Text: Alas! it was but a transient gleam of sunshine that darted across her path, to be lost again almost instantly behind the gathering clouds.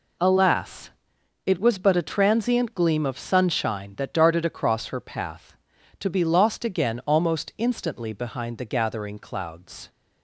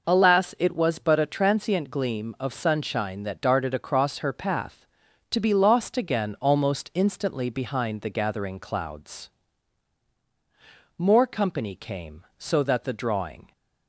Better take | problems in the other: first | goes on to say "More company came so that the drawing"; strong; from 10.9 s on; 2.5 s long

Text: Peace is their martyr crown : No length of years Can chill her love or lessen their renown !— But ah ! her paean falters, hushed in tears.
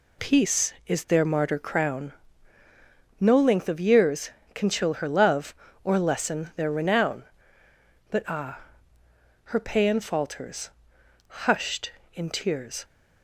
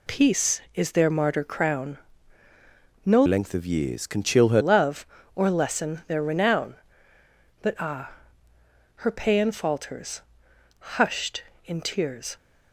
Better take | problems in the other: first | changes voice from "length" to "her"; from 3.2 to 4.6 s; 1.4 s long

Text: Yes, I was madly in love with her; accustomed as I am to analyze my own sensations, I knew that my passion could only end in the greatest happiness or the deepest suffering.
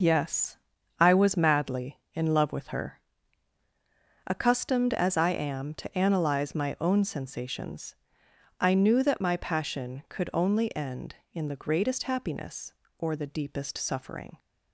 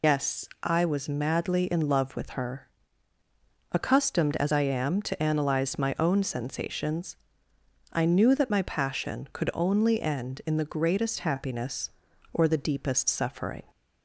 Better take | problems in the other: first | loses the start of "Yes"; at 0.0 s; 65 ms

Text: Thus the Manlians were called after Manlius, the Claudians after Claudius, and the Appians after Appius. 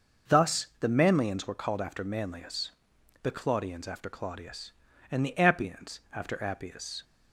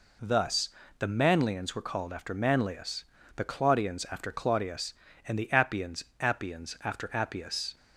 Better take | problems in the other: first | pauses between "Thus" and "the"; slight; at 0.6 s; 0.30 s long // says "Appians" twice; at 6.1 s

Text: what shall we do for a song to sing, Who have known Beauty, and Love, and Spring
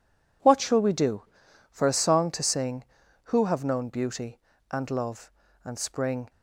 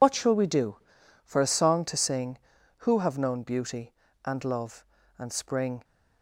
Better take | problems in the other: first | loses the start of "what"; at 0.0 s; 65 ms

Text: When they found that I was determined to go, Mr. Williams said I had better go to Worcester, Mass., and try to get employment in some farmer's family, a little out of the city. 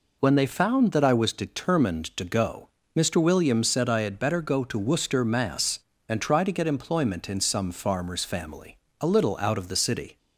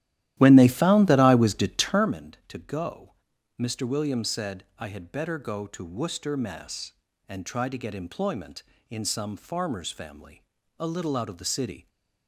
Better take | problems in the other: first | starts louder than the rest; strong; until 2.1 s; 13.5 dB

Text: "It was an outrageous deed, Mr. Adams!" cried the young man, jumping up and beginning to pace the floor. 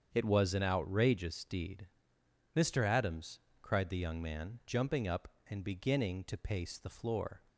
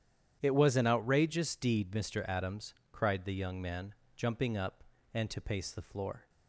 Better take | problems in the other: first | starts louder than the rest; strong; until 1.4 s; 9.5 dB; strong in the first // skips "beginning"; at 5.2 s

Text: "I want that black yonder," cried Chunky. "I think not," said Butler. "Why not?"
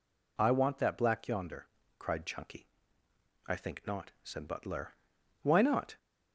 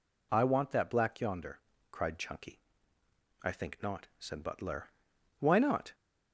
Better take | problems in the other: neither | none

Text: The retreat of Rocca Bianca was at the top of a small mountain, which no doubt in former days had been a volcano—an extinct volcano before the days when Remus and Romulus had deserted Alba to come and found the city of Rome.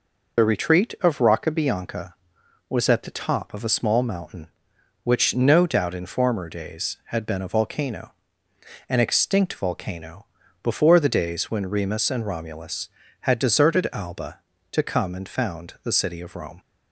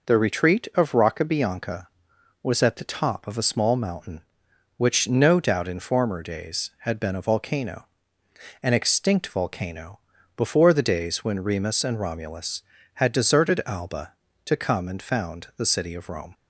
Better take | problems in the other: second | loses the start of "The"; at 0.3 s; 40 ms // pauses between "volcano" and "before"; slight; at 10.2 s; 0.36 s long; slight in the second

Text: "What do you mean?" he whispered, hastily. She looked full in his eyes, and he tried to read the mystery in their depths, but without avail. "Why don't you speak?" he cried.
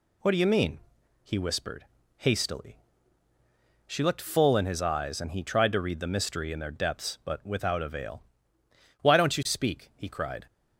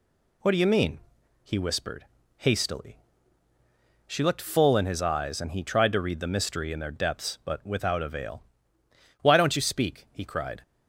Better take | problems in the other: neither | none

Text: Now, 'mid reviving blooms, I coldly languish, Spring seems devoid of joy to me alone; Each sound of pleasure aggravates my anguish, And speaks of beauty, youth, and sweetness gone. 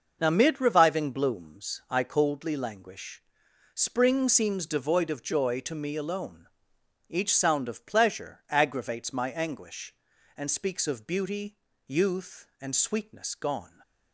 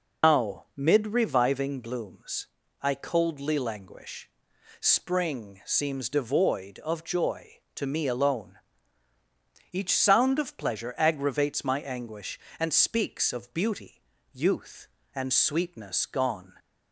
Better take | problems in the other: first | loses the start of "Now"; at 0.2 s; 130 ms

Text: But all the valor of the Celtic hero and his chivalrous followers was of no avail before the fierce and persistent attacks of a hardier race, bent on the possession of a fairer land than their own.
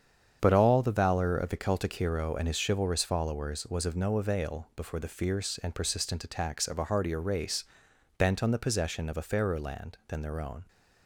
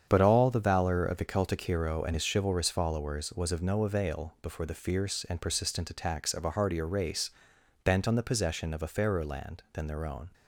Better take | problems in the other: neither | starts louder than the rest; strong; the same in both

